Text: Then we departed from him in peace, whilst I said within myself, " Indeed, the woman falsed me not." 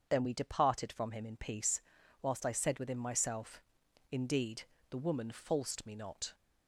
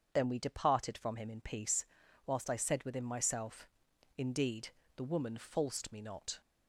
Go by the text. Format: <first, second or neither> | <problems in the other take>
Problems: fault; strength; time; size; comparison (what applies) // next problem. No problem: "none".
neither | starts louder than the rest; strong; the same in both